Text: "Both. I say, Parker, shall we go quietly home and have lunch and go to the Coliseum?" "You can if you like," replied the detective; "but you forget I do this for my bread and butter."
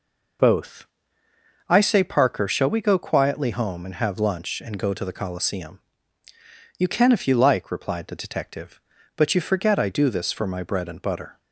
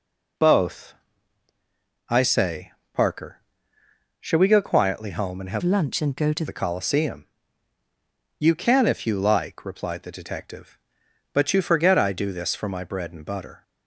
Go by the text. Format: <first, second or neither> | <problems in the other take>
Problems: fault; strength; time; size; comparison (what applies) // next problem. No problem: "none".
first | changes voice from "lunch" to "to"; from 5.6 to 6.4 s; 0.8 s long